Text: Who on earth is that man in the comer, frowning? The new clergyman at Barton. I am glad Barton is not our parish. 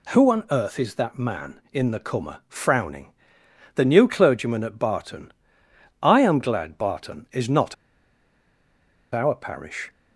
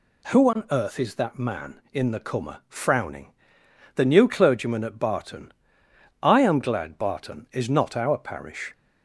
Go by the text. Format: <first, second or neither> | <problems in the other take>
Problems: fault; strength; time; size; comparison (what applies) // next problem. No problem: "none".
second | pauses between "not" and "our"; strong; at 7.7 s; 1.3 s long